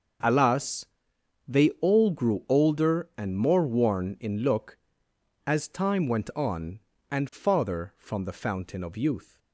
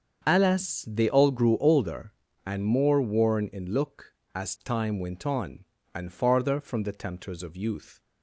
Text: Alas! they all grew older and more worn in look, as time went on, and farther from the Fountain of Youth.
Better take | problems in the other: first | starts louder than the rest; strong; until 1.2 s; 7 dB; also in the first // says "Tempters" for "Fountain"; at 6.9 s

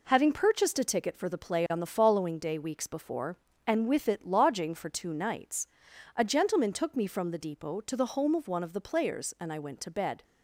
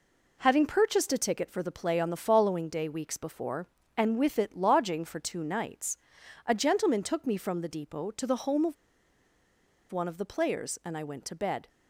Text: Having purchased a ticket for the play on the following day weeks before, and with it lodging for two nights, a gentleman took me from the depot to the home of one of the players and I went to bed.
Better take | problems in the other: first | pauses between "of" and "one"; at 8.7 s; 1.1 s long

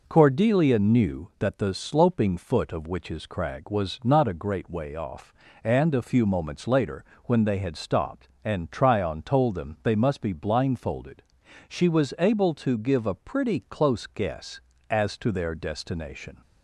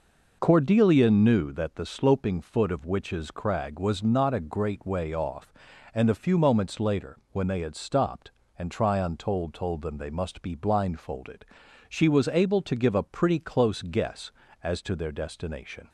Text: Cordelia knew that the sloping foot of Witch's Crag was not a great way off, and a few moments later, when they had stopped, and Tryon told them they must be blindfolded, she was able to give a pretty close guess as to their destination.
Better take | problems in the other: first | says "told" twice; at 9.5 s

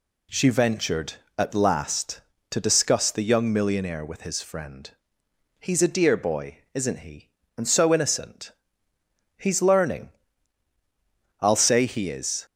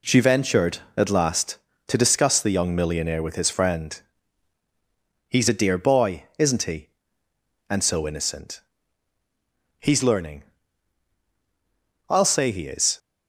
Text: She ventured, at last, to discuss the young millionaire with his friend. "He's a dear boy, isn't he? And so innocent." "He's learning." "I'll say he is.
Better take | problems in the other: first | gets quieter; noticeable; throughout; 5.5 dB

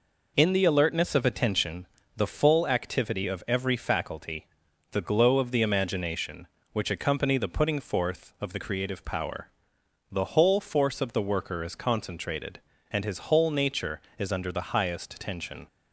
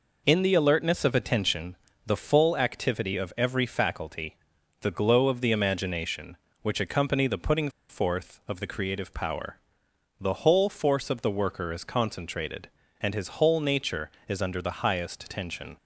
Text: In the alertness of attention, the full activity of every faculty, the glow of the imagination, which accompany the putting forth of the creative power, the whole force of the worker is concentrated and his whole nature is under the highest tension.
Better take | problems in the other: first | pauses between "putting" and "forth"; slight; at 7.6 s; 0.20 s long

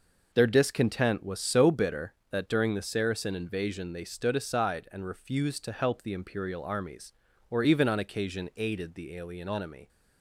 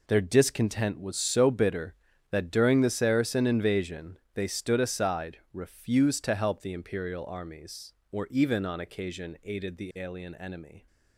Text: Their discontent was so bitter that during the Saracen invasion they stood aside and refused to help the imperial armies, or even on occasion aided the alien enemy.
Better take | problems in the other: first | pauses between "invasion" and "they"; slight; at 4.1 s; 0.16 s long // skips "and"; at 5.4 s

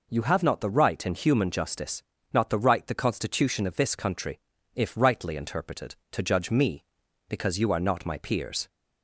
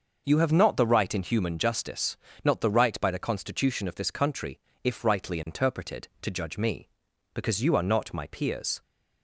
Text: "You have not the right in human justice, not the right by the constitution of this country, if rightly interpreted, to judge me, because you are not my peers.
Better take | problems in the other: second | skips "by"; at 2.8 s

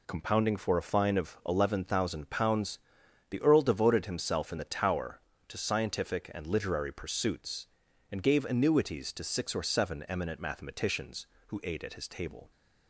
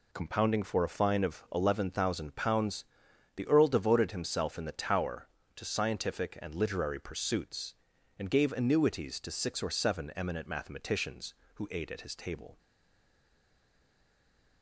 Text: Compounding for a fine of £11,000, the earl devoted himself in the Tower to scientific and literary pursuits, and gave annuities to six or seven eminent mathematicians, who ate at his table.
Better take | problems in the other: first | stays silent after the last word; noticeable; from 12.5 s on; 2.1 s long

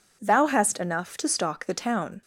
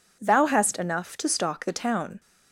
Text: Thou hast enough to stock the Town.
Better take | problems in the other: neither | none

